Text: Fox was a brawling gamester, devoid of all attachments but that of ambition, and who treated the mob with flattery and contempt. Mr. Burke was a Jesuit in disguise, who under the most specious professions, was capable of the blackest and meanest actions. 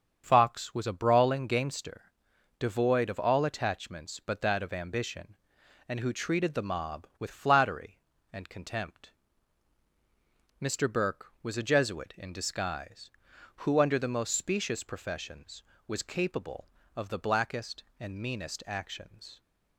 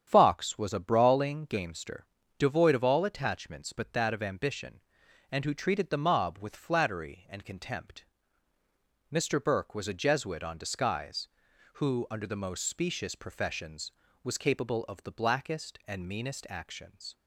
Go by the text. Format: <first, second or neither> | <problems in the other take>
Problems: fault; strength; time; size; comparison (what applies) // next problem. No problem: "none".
first | starts louder than the rest; strong; until 1.0 s; 9 dB; strong in the first // says "on" for "in"; at 10.4 s